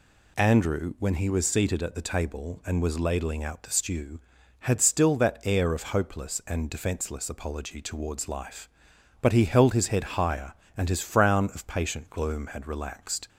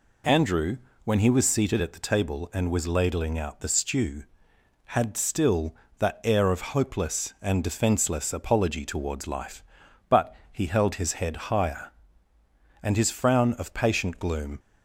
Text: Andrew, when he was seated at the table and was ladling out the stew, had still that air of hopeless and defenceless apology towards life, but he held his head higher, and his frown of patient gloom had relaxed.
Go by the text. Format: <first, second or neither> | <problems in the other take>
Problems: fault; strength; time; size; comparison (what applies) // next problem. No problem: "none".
first | pauses between "but" and "he"; slight; at 10.3 s; 0.16 s long // stops before "had relaxed"; at 14.5 s